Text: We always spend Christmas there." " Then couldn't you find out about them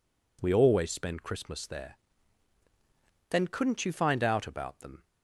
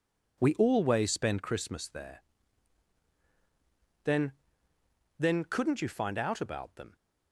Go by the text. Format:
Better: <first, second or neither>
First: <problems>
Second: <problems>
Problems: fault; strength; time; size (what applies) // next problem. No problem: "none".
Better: first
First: none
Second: says "Then" twice; at 5.1 s